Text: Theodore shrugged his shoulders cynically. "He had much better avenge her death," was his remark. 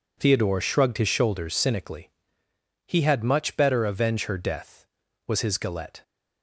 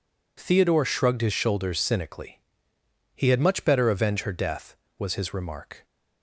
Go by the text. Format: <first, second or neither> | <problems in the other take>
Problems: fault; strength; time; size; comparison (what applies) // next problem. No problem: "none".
second | says "galette" for "remark"; at 5.5 s